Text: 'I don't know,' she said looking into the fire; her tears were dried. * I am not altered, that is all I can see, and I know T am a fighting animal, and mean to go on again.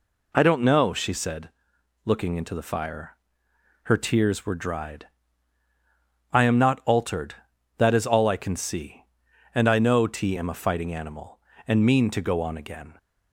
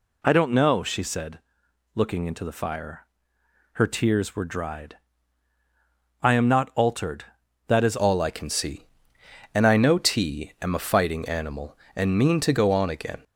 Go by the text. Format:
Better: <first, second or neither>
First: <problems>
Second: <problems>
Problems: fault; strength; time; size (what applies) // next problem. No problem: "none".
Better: first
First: pauses between "said" and "looking"; noticeable; at 1.4 s; 0.54 s long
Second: pauses between "said" and "looking"; noticeable; at 1.3 s; 0.54 s long // changes voice at "all"; from 7.9 s on; 5.3 s long